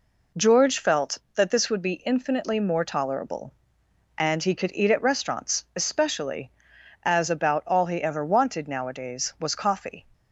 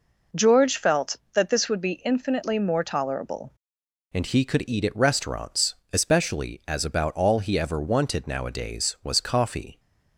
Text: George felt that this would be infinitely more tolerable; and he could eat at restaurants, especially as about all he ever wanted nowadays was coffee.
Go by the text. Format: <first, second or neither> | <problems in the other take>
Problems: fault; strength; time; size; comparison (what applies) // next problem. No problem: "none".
first | changes voice at "and"; from 4.1 s on; 5.6 s long